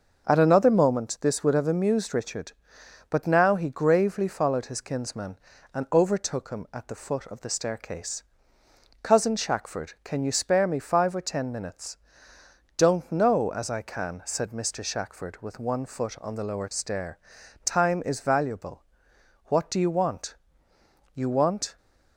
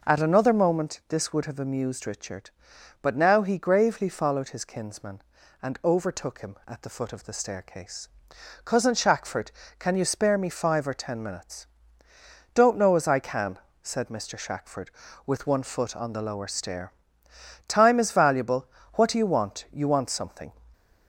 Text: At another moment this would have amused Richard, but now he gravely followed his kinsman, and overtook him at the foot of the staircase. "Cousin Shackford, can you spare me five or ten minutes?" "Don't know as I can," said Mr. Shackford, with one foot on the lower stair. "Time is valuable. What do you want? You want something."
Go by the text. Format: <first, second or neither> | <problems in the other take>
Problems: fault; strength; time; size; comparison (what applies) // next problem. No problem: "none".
second | starts louder than the rest; until 1.2 s; 6.5 dB // stops before "something"; at 21.7 s